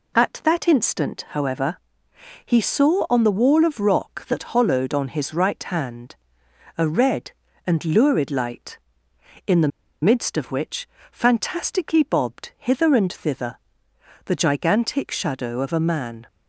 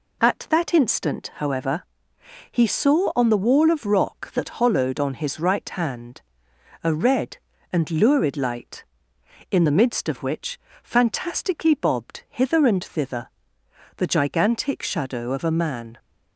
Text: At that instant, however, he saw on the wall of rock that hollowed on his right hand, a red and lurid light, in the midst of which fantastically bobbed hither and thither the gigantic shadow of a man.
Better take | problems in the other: second | pauses between "the" and "midst"; slight; at 9.7 s; 0.34 s long // pauses between "which" and "fantastically"; slight; at 10.8 s; 0.24 s long; slight in the second // pauses between "thither" and "the"; noticeable; at 13.5 s; 0.70 s long; noticeable in the second

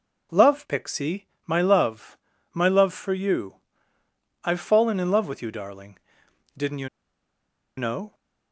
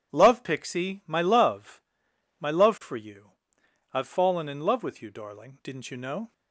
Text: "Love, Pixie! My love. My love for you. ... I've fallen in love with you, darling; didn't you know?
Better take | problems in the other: second | pauses between "you" and "know"; noticeable; at 6.8 s; 0.89 s long

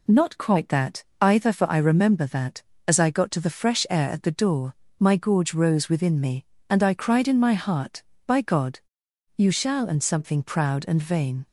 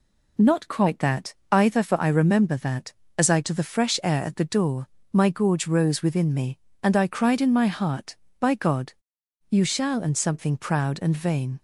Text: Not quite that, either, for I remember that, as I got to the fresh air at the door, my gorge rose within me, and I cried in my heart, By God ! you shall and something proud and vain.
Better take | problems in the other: first | skips "got"; at 3.4 s

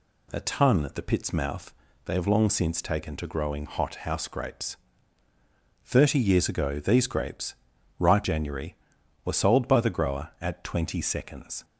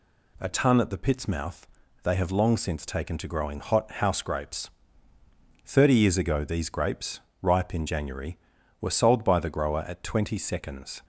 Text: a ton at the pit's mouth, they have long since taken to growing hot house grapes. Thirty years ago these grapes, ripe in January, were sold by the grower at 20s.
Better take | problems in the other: second | skips "in"; at 8.2 s

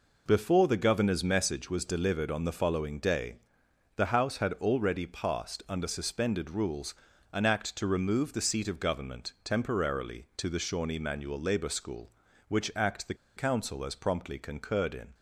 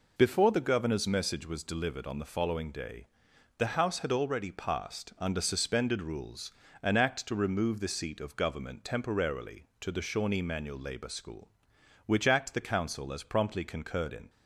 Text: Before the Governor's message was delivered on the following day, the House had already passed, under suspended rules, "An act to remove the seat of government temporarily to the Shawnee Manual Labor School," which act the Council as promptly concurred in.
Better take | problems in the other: second | pauses between "the" and "Council"; slight; at 13.1 s; 0.21 s long

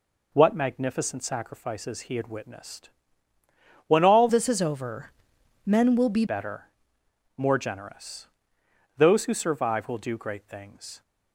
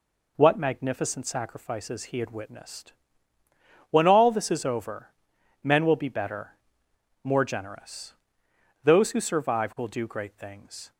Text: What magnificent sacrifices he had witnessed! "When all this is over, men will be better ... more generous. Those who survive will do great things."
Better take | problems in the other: second | changes voice from "this" to "be"; from 4.2 to 6.2 s; 2.0 s long

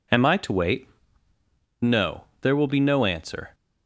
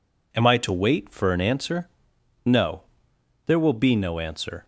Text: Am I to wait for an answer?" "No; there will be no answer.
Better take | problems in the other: second | skips "for an answer"; at 1.3 s

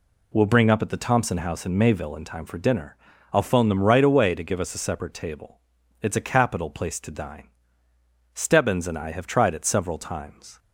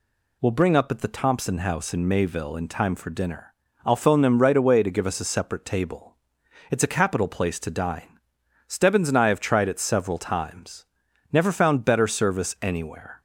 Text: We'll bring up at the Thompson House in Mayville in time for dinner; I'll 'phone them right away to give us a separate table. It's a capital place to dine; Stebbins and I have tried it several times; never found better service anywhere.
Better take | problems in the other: second | stops before "never found better service anywhere"; at 10.5 s

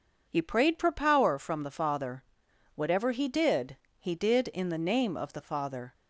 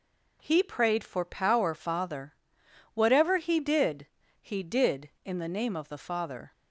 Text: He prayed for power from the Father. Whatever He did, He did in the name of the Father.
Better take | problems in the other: first | skips "from the"; at 1.7 s

